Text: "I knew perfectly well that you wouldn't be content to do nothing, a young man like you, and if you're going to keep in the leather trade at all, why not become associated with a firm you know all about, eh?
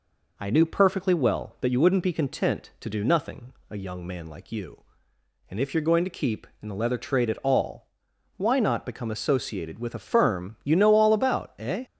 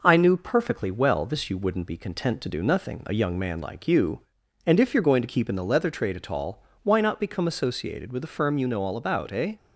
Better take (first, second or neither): first